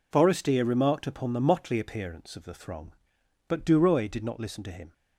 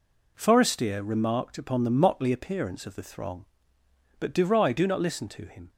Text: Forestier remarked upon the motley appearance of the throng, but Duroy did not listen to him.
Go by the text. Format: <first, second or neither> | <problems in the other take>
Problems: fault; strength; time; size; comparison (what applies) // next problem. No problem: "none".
first | says "do" for "did"; at 4.7 s